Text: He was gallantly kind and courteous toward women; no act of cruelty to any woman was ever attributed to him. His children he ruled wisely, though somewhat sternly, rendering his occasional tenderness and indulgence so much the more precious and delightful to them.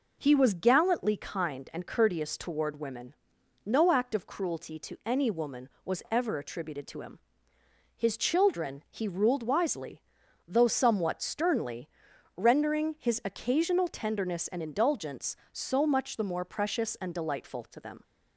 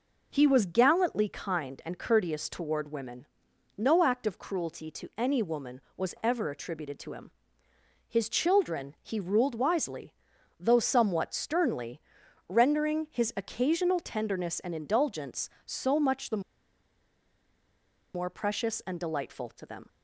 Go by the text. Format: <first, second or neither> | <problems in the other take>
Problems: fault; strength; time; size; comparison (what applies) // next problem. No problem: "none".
first | pauses between "the" and "more"; strong; at 16.4 s; 1.7 s long